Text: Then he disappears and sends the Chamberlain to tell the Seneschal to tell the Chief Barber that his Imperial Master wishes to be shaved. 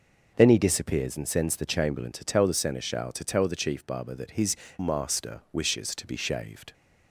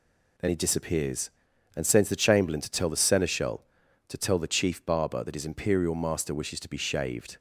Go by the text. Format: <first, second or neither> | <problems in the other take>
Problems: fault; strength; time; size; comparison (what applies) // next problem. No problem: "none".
second | skips "Imperial"; at 4.6 s